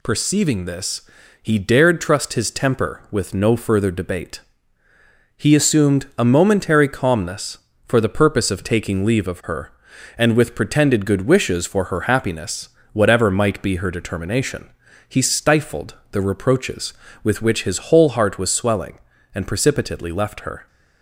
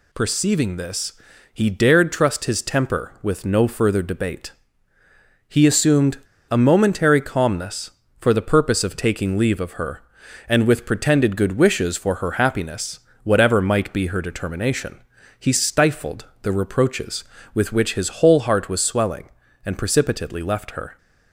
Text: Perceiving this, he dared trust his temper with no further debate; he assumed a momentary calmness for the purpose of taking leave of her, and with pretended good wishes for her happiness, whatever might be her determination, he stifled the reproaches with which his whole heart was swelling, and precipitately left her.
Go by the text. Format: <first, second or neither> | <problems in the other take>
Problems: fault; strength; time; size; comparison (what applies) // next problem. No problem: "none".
first | pauses between "assumed" and "a"; slight; at 6.1 s; 0.31 s long // pauses between "stifled" and "the"; slight; at 16.2 s; 0.18 s long; slight in the first